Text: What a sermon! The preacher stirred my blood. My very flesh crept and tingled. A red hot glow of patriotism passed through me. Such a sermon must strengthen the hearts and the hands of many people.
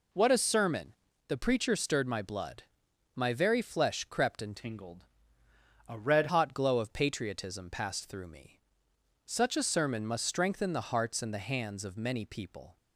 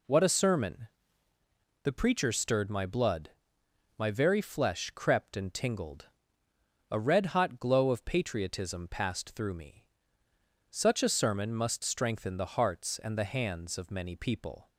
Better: second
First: changes voice from "tingled" to "red"; from 4.5 to 6.2 s; 1.7 s long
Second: none

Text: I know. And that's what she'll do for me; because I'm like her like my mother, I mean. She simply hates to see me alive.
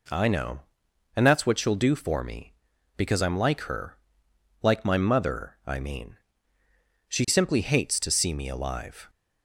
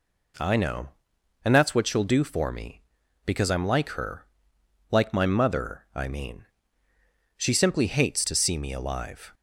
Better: neither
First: pauses between "her" and "like"; noticeable; at 3.9 s; 0.68 s long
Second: pauses between "her" and "like"; noticeable; at 4.2 s; 0.68 s long

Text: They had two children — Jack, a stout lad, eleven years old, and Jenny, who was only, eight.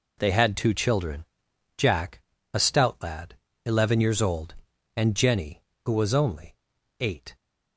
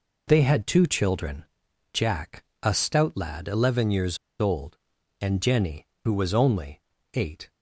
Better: first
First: none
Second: pauses between "years" and "old"; slight; at 4.1 s; 0.23 s long

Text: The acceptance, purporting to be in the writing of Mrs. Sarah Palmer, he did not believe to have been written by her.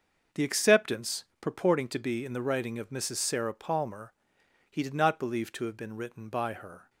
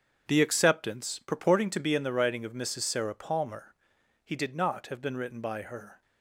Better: first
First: starts louder than the rest; until 1.5 s; 6.5 dB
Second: starts louder than the rest; until 1.2 s; 7 dB // skips "believe to"; at 4.8 s

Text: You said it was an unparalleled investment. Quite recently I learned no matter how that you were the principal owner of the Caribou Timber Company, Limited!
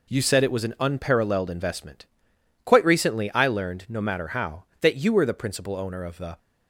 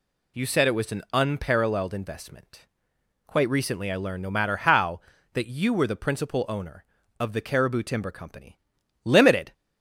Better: second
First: stops before "Caribou Timber Company Limited"; at 6.3 s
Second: none

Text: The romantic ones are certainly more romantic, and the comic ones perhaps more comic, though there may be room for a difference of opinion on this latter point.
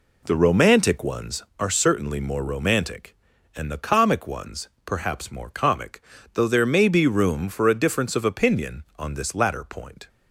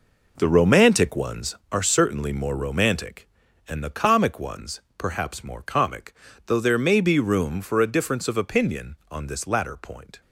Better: first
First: pauses between "ones" and "perhaps"; slight; at 4.6 s; 0.16 s long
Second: gets quieter; strong; throughout; 10 dB // pauses between "ones" and "perhaps"; slight; at 4.8 s; 0.16 s long

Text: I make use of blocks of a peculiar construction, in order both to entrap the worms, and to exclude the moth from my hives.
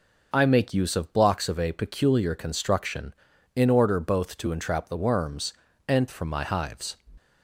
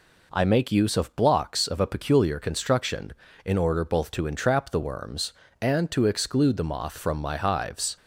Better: second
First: skips "to exclude the moth"; at 6.0 s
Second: none

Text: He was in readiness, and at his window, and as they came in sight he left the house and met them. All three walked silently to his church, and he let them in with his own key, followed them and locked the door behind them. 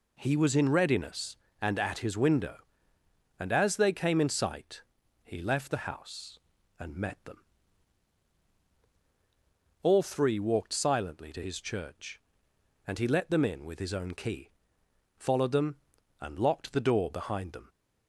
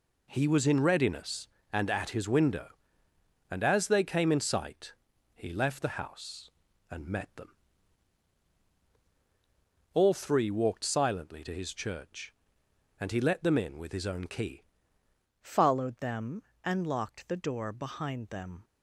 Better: first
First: pauses between "sight" and "he"; at 4.8 s; 0.42 s long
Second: pauses between "sight" and "he"; at 4.9 s; 0.42 s long // changes voice at "followed"; from 15.4 s on; 3.2 s long

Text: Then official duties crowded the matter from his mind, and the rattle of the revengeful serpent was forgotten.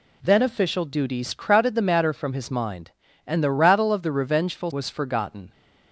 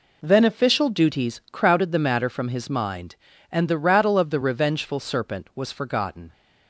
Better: second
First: skips "serpent"; at 4.7 s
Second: none

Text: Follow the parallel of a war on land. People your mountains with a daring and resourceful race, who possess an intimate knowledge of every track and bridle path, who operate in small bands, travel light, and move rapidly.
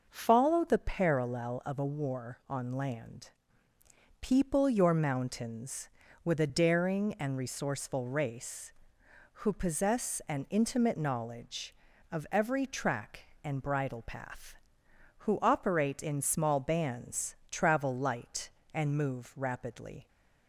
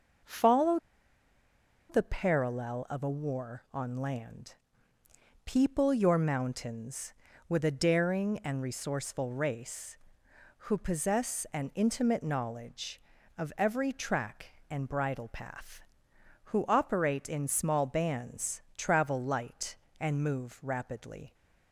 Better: first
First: none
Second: pauses between "Follow" and "the"; at 0.7 s; 1.1 s long

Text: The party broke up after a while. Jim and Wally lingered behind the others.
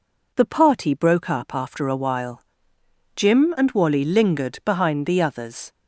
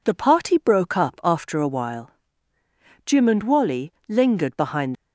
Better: first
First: none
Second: pauses between "Wally" and "lingered"; slight; at 3.9 s; 0.16 s long // stops before "the others"; at 4.9 s

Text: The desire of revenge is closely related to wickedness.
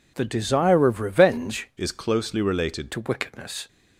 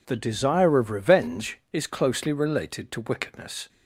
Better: second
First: changes voice from "is" to "related"; from 1.7 to 2.9 s; 1.2 s long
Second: none

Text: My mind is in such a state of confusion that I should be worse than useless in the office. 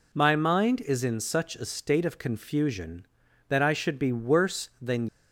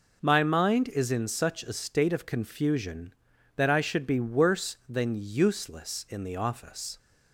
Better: second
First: stops before "useless in the office"; at 5.0 s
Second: none

